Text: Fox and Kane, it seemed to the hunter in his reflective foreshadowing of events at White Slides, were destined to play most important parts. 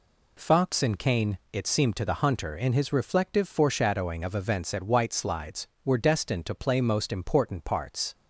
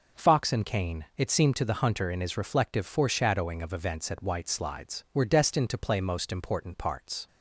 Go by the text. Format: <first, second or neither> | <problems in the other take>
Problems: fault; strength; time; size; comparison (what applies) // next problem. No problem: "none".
neither | none